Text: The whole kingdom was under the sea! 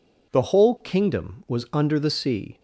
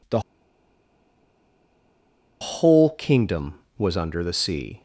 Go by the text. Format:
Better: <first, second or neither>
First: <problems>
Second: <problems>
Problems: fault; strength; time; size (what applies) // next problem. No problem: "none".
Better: first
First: none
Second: pauses between "The" and "whole"; strong; at 0.1 s; 2.2 s long